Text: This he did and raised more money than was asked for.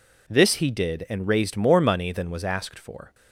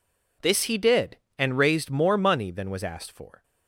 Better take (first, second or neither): neither